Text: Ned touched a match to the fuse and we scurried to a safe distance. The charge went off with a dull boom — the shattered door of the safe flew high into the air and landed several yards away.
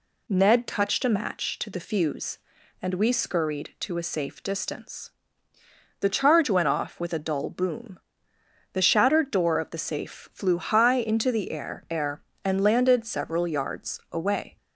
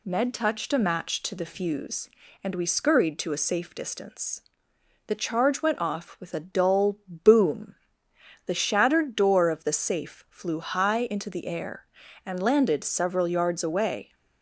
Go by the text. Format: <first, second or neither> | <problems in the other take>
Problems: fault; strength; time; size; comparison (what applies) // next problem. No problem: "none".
second | says "air" twice; at 11.8 s